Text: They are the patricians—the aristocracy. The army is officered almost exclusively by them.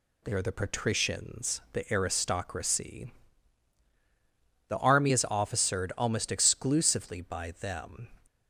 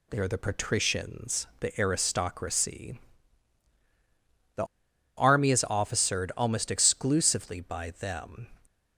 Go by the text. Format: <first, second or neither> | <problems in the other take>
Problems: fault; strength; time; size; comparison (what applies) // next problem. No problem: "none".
first | pauses between "The" and "army"; noticeable; at 4.6 s; 0.52 s long